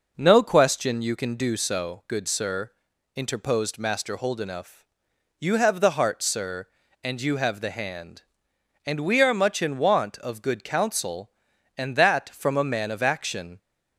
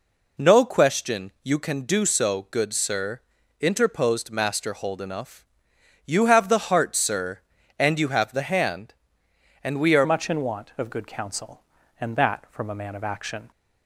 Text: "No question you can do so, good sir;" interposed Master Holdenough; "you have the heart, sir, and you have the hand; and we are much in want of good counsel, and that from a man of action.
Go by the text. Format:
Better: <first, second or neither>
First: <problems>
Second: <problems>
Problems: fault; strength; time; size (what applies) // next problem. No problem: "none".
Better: first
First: none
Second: changes voice at "much"; from 10.0 s on; 3.5 s long